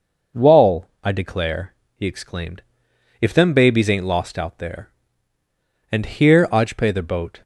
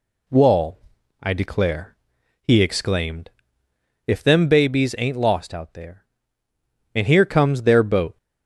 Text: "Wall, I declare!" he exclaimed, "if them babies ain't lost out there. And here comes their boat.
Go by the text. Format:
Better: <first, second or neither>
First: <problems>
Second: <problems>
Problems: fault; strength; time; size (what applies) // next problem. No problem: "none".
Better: second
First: says "ajpe" for "comes"; at 6.4 s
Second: none